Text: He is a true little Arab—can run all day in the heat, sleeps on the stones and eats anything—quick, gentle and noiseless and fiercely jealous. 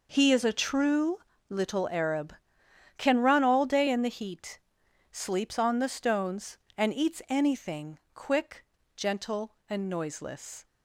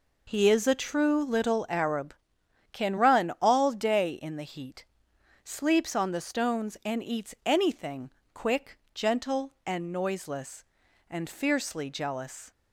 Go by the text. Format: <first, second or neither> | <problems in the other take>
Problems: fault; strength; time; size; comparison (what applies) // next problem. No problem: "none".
second | pauses between "true" and "little"; slight; at 1.2 s; 0.28 s long // stops before "and fiercely jealous"; at 10.6 s